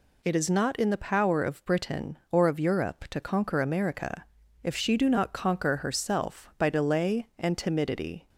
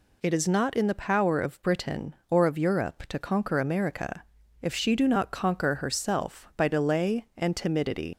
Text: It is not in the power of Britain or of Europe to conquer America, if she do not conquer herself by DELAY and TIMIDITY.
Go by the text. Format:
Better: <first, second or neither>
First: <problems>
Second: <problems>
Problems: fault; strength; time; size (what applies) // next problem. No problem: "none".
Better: first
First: none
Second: leaves "TIMIDITY" unfinished; at 8.1 s; 140 ms